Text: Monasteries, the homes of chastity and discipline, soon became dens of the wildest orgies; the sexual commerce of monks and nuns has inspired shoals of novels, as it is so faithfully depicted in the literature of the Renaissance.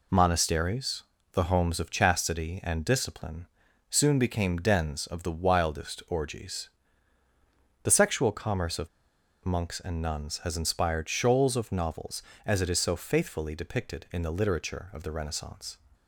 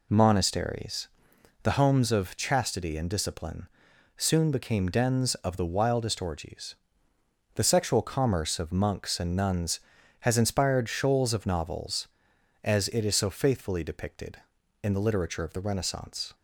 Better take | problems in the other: second | pauses between "of" and "monks"; noticeable; at 8.8 s; 0.57 s long

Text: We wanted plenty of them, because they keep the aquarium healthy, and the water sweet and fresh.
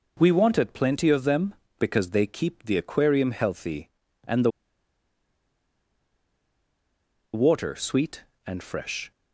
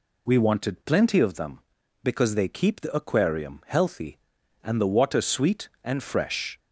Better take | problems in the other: second | pauses between "the" and "water"; strong; at 4.4 s; 2.8 s long

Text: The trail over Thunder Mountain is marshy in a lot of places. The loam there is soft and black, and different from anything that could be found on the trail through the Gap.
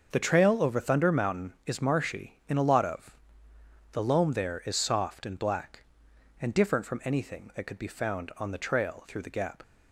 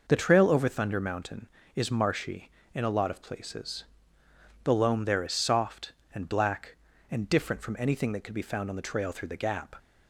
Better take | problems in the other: second | starts louder than the rest; noticeable; until 1.1 s; 6 dB // skips "places"; at 3.5 s

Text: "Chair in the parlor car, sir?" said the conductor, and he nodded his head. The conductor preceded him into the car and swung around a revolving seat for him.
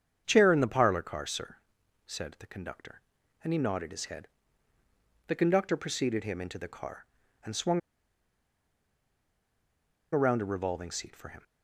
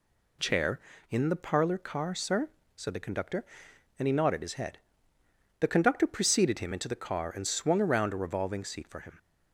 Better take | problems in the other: second | starts louder than the rest; strong; until 1.2 s; 7.5 dB // pauses between "swung" and "around"; strong; at 7.7 s; 2.3 s long

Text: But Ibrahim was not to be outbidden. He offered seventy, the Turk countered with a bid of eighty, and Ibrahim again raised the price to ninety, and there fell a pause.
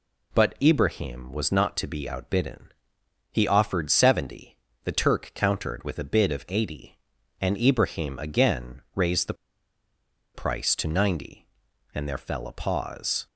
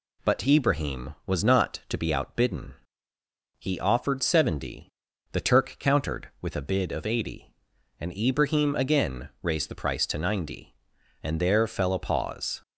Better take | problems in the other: second | pauses between "the" and "price"; at 9.3 s; 1.0 s long

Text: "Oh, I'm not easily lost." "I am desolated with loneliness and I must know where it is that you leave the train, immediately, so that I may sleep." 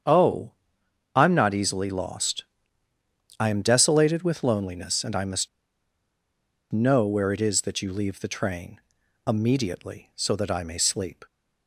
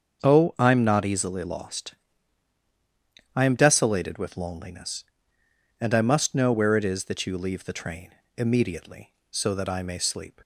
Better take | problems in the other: second | starts louder than the rest; strong; until 1.6 s; 8 dB; also in the second // pauses between "must" and "know"; strong; at 5.4 s; 1.2 s long

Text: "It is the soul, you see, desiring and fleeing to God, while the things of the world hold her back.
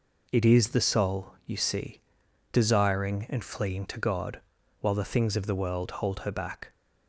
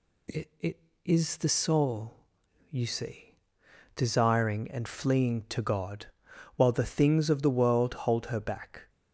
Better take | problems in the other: first | says "It" twice; at 0.6 s

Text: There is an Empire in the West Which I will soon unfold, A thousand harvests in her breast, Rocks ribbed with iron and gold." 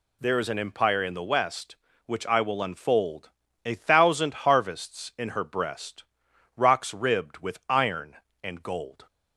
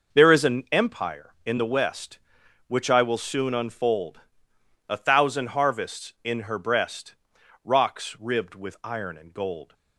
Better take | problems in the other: second | skips "soon"; at 2.6 s

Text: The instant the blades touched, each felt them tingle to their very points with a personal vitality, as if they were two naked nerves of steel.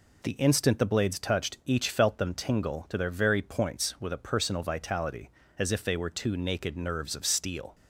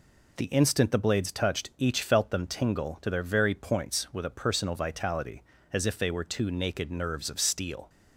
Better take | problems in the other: neither | none

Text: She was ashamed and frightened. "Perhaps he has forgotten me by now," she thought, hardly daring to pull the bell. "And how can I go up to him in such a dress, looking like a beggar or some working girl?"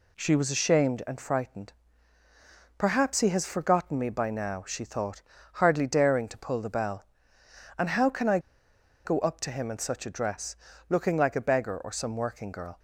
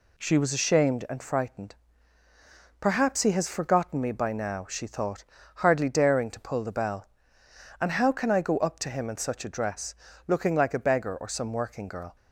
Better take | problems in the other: second | pauses between "I" and "go"; noticeable; at 8.3 s; 0.65 s long

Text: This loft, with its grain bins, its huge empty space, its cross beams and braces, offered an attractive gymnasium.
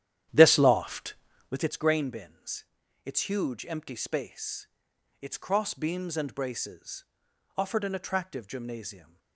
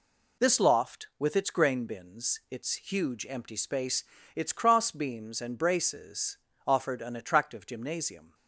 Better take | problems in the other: second | starts louder than the rest; strong; until 1.7 s; 11 dB

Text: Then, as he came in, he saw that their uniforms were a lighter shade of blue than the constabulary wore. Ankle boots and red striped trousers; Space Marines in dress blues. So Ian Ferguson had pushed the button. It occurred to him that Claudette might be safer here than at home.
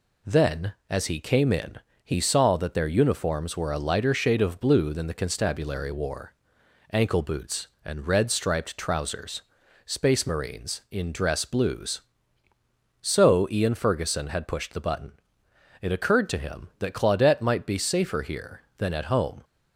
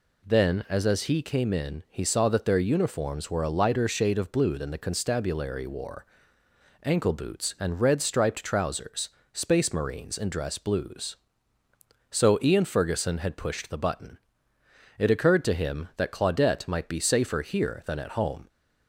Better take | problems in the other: first | says "as" twice; at 0.8 s

